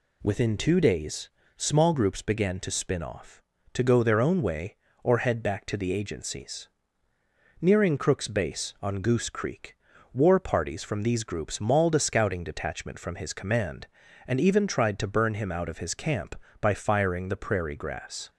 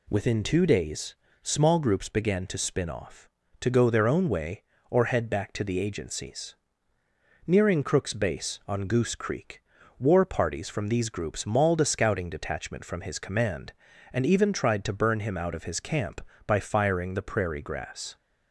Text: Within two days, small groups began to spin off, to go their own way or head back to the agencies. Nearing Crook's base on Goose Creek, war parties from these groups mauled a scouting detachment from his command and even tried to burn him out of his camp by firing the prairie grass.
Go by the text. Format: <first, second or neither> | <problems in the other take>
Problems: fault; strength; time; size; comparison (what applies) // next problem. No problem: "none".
neither | none